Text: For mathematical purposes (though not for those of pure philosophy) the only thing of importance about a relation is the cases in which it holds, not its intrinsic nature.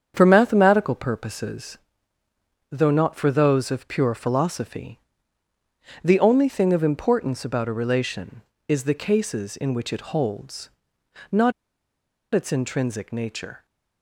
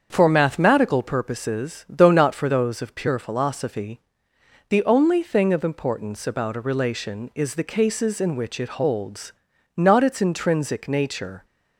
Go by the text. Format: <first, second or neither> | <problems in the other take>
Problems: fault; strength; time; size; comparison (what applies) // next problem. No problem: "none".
second | starts louder than the rest; strong; until 1.1 s; 7.5 dB; strong in the second // pauses between "not" and "its"; noticeable; at 11.5 s; 0.81 s long